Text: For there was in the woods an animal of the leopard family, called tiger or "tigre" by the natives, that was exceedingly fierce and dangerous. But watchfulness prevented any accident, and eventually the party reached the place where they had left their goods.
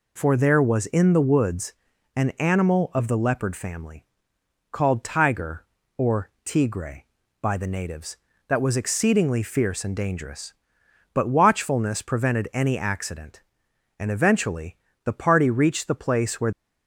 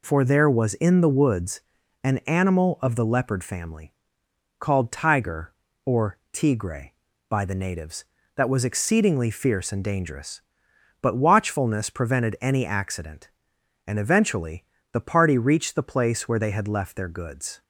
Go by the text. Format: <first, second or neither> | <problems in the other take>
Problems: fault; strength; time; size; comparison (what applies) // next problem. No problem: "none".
second | pauses between "woods" and "an"; at 1.7 s; 0.40 s long; also in the second // pauses between "eventually" and "the"; slight; at 14.7 s; 0.28 s long; slight in the second // stops before "they had left their goods"; at 16.5 s